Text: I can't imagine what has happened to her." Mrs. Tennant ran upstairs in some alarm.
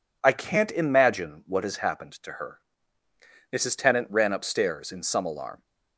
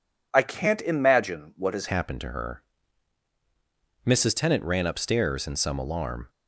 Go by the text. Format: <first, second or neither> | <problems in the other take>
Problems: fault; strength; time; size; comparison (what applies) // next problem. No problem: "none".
first | changes voice at "happened"; from 1.8 s on; 4.4 s long